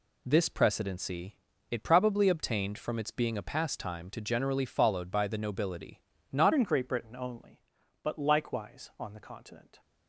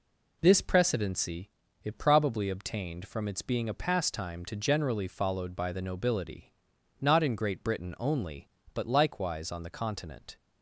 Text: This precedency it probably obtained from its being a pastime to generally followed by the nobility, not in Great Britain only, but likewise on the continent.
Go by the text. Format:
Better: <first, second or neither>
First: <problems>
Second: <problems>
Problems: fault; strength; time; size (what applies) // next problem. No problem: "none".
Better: second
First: pauses between "precedency" and "it"; slight; at 1.3 s; 0.36 s long // changes voice at "in"; from 6.5 s on; 3.3 s long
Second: pauses between "precedency" and "it"; slight; at 1.4 s; 0.34 s long